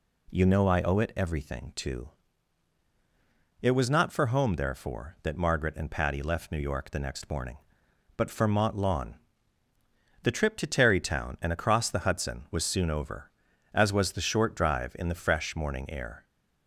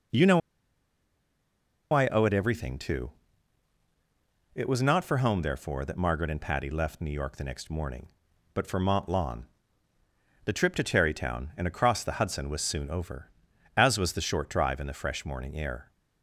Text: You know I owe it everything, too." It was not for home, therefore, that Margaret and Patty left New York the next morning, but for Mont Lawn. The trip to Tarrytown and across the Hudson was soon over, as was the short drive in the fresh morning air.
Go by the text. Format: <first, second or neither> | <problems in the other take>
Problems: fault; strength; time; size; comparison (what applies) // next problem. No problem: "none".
first | pauses between "know" and "I"; strong; at 0.4 s; 1.5 s long